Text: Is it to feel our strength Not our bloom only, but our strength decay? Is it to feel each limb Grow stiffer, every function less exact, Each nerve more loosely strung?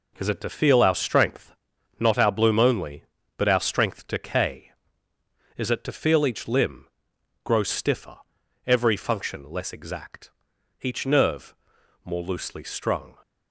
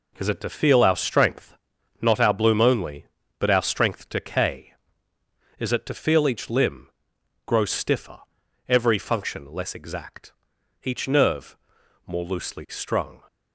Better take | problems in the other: neither | pauses between "strength" and "Not"; the same in both // pauses between "limb" and "Grow"; noticeable; the same in both // pauses between "nerve" and "more"; noticeable; the same in both

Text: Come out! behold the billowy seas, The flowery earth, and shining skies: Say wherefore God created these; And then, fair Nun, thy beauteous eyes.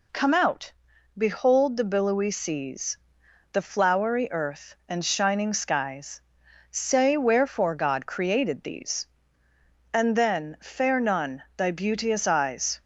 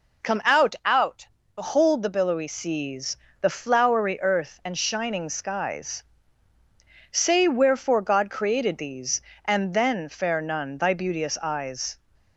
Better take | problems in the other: first | says "out" twice; at 0.8 s

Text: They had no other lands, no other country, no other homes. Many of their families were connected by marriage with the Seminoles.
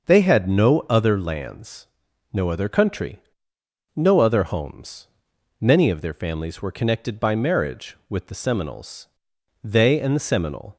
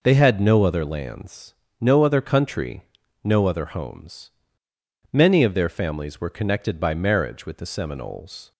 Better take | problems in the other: second | starts louder than the rest; until 1.1 s; 6 dB // goes on to say "They and the Seminole"; noticeable; from 9.6 s on; 1.1 s long

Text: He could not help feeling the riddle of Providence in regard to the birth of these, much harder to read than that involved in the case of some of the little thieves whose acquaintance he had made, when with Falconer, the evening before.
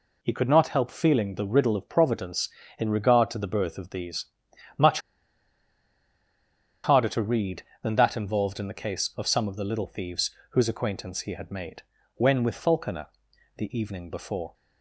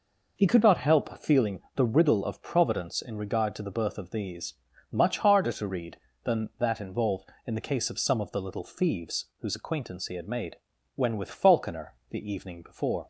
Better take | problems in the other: second | pauses between "much" and "harder"; strong; at 5.0 s; 1.8 s long // pauses between "thieves" and "whose"; slight; at 10.2 s; 0.22 s long

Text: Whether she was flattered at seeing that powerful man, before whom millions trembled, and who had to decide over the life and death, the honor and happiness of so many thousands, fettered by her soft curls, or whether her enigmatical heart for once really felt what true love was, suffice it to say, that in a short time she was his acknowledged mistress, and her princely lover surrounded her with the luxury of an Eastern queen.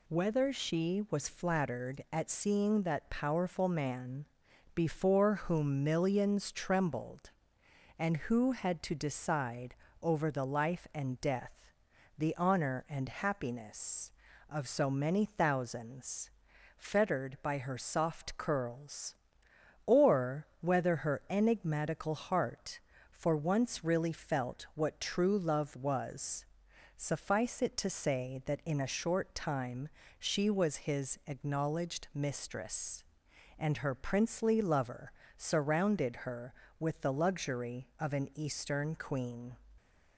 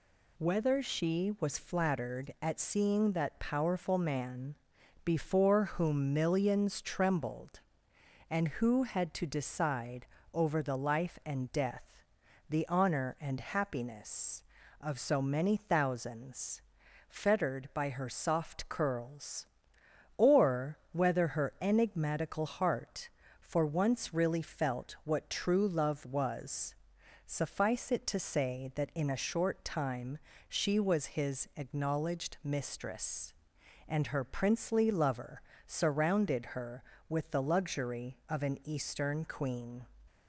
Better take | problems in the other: neither | pauses between "decide" and "over"; slight; the same in both // pauses between "or" and "whether"; slight; the same in both // pauses between "time" and "she"; slight; the same in both // pauses between "lover" and "surrounded"; slight; the same in both

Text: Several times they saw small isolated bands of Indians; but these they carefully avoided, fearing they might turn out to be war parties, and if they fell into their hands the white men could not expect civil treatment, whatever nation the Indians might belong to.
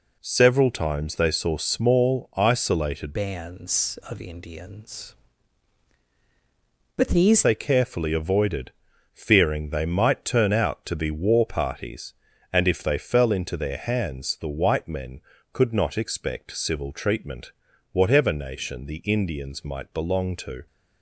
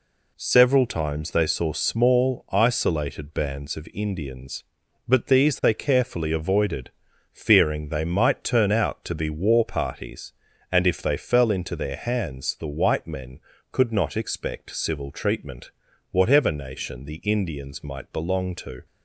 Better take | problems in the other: second | changes voice from "bands" to "these"; from 3.1 to 7.4 s; 4.3 s long

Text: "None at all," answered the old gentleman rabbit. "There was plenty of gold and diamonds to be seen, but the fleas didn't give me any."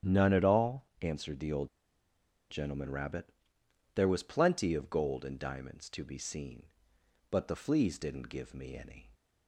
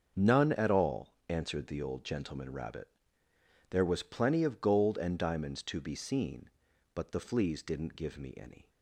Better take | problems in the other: second | starts louder than the rest; strong; until 1.2 s; 9.5 dB; also in the second // pauses between "old" and "gentleman"; noticeable; at 1.6 s; 0.82 s long

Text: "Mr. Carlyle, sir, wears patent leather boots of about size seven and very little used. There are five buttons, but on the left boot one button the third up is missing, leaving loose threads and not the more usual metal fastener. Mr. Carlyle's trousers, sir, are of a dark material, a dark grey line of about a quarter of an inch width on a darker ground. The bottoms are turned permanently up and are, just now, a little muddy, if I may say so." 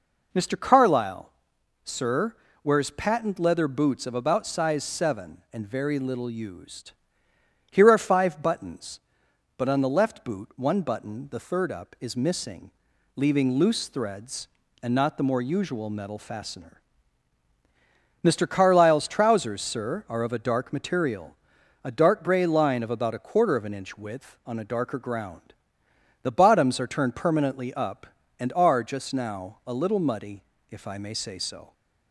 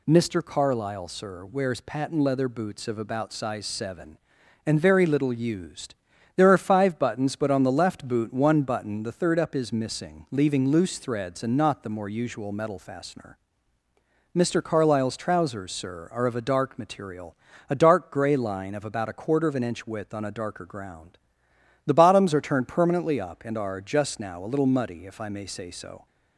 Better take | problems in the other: second | says "Here" for "There"; at 7.7 s

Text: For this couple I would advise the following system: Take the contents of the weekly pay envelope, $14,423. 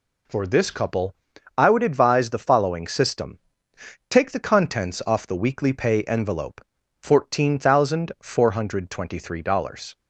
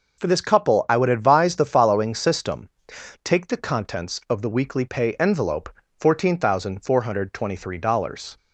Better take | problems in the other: second | pauses between "couple" and "I"; at 1.1 s; 0.42 s long // says "off" for "of"; at 5.0 s

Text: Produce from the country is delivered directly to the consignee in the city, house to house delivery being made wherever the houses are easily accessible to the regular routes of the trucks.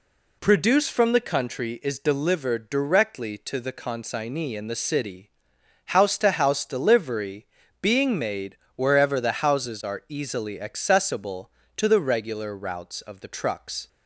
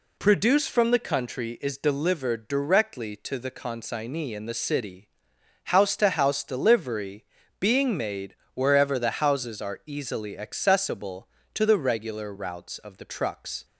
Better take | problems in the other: neither | pauses between "delivery" and "being"; slight; the same in both // pauses between "made" and "wherever"; slight; the same in both

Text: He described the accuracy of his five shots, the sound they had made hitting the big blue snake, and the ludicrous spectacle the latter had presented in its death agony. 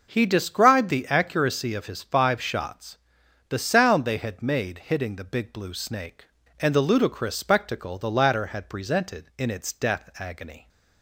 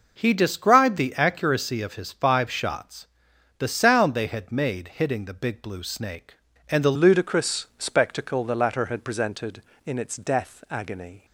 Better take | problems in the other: first | changes voice at "ludicrous"; from 6.9 s on; 4.3 s long

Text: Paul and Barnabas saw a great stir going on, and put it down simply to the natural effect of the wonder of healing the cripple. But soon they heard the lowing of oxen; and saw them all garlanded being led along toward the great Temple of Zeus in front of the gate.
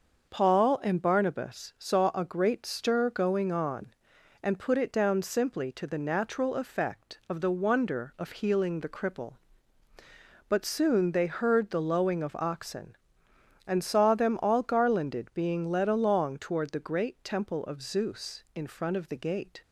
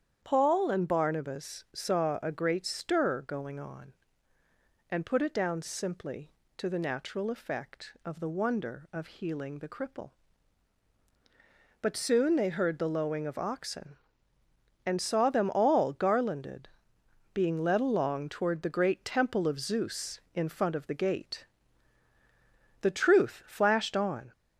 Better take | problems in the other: first | starts louder than the rest; strong; until 1.2 s; 8.5 dB; also in the first // pauses between "garlanded" and "being"; noticeable; at 16.6 s; 0.66 s long // goes on to say "The truth flashed on"; from 22.8 s on; 1.5 s long

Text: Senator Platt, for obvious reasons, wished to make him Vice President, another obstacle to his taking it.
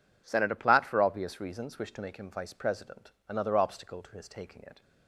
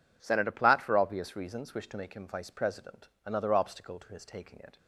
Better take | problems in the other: neither | none

